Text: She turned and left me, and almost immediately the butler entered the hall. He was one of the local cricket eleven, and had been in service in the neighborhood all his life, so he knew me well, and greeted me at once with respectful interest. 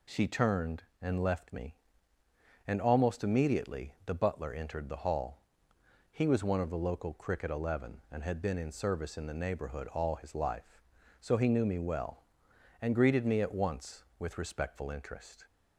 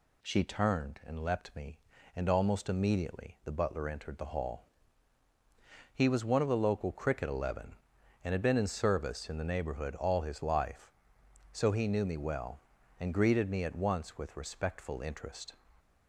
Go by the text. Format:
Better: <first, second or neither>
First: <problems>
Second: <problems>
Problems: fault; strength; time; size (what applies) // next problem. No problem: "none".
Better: first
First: none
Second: says "leapt" for "left"; at 1.2 s